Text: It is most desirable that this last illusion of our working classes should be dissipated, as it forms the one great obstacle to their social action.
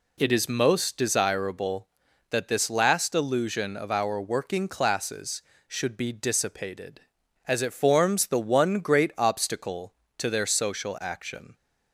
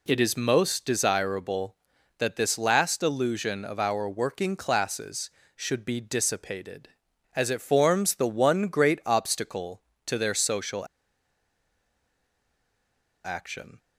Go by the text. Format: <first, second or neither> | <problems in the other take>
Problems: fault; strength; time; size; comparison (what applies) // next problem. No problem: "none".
first | pauses between "social" and "action"; strong; at 10.8 s; 2.3 s long